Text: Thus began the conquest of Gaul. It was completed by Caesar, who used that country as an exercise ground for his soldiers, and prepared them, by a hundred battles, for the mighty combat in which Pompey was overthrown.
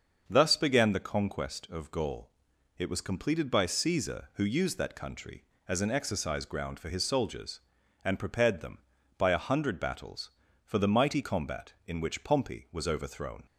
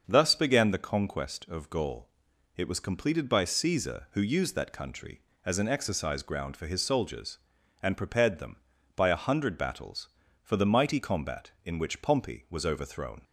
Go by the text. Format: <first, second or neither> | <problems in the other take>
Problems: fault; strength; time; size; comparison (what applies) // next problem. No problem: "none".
neither | starts louder than the rest; the same in both